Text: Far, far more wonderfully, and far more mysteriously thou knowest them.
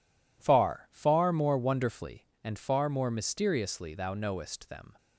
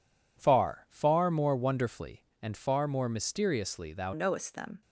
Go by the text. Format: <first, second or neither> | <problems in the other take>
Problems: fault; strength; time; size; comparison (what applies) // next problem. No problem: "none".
first | changes voice at "knowest"; from 4.1 s on; 0.7 s long